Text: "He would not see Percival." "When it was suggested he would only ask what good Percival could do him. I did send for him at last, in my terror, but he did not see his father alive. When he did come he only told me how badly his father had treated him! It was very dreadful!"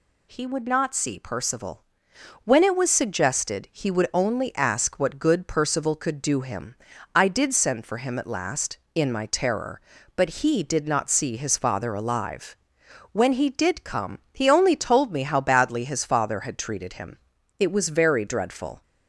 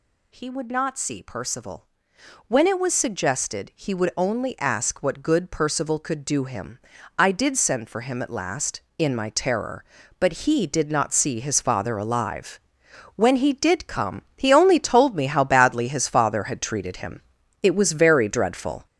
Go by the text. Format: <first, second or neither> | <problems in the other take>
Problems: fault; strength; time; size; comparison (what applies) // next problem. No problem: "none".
first | gets louder; throughout; 6.5 dB // pauses between "come" and "he"; slight; at 14.2 s; 0.16 s long; slight in the first